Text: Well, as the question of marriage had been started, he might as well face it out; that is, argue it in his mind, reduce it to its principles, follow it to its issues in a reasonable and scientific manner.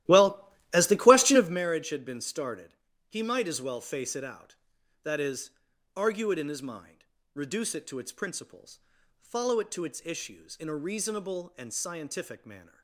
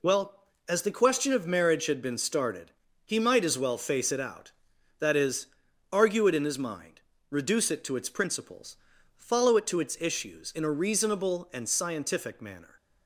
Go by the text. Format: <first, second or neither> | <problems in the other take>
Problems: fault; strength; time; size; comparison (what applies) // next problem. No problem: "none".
second | starts louder than the rest; strong; until 1.6 s; 14.5 dB